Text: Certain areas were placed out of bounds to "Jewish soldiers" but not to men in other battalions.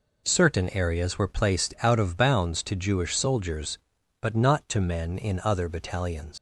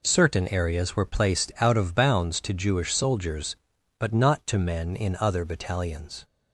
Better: second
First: leaves "battalions" unfinished; at 6.3 s; 105 ms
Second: none

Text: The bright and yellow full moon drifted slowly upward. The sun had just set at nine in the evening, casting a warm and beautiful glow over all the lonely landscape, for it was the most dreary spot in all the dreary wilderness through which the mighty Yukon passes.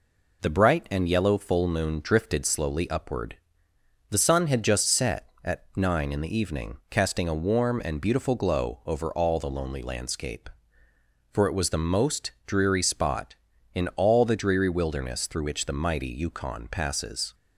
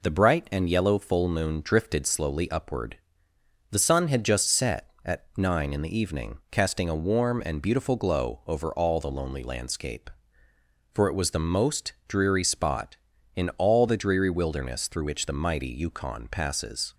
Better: neither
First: none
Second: none

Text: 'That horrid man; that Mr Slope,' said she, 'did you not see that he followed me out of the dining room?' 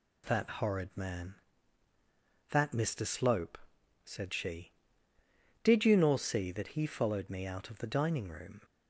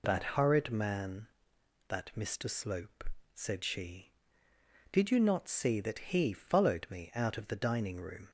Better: second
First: says "nor" for "not"; at 5.9 s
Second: none

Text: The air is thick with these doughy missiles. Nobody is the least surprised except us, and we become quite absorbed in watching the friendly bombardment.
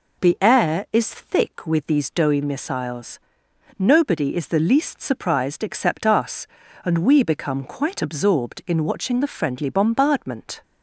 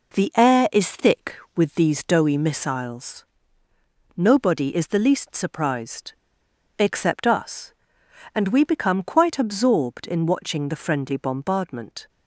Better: first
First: none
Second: pauses between "surprised" and "except"; noticeable; at 6.1 s; 0.65 s long

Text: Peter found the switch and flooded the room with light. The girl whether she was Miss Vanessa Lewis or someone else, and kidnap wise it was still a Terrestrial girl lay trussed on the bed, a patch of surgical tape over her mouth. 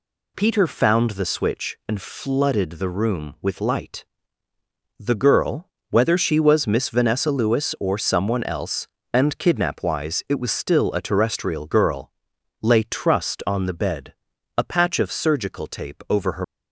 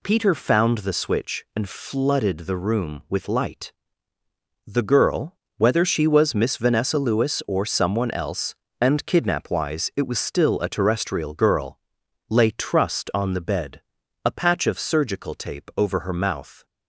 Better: second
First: pauses between "girl" and "whether"; slight; at 5.6 s; 0.24 s long // pauses between "girl" and "lay"; noticeable; at 12.1 s; 0.50 s long // stops before "mouth"; at 16.4 s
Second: pauses between "girl" and "whether"; slight; at 5.3 s; 0.24 s long // pauses between "girl" and "lay"; noticeable; at 11.7 s; 0.50 s long

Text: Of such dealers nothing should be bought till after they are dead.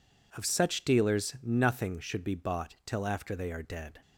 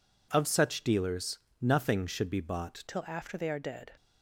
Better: first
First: none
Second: pauses between "dealers" and "nothing"; slight; at 1.3 s; 0.20 s long // changes voice at "till"; from 2.8 s on; 1.1 s long

